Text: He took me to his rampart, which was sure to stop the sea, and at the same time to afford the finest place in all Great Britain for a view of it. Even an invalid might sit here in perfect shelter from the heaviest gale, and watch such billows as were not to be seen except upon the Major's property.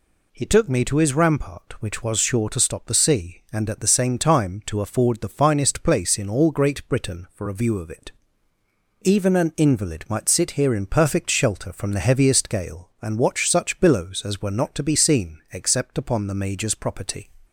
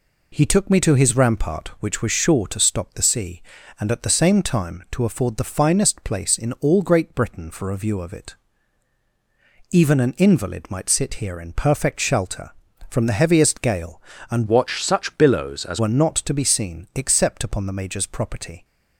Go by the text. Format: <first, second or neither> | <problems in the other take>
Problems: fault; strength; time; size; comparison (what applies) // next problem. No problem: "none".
first | changes voice from "watch" to "as"; from 14.4 to 15.7 s; 1.3 s long